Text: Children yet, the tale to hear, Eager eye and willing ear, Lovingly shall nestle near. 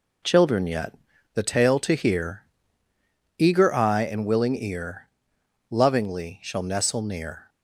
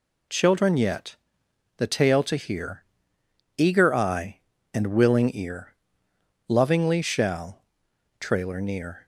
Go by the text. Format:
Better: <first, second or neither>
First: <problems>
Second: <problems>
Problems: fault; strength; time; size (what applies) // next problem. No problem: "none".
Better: first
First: none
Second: says "trailer" for "nestle"; at 8.1 s